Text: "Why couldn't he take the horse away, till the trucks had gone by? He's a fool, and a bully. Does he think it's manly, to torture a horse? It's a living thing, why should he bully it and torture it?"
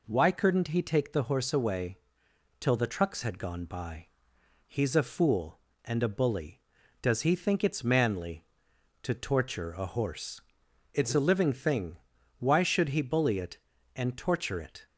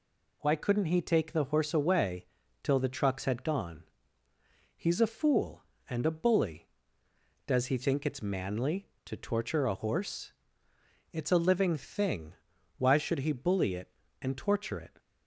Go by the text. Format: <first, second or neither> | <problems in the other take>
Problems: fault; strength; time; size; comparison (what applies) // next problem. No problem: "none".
first | skips "by"; at 4.2 s